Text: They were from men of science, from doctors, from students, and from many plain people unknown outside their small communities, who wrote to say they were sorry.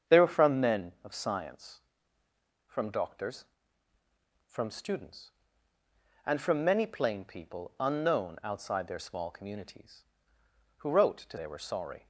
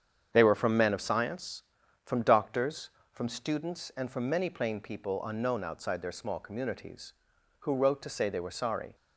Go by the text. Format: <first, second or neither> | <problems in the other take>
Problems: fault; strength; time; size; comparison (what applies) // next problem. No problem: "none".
second | starts louder than the rest; strong; until 1.2 s; 7.5 dB; strong in the second // skips "say"; at 11.3 s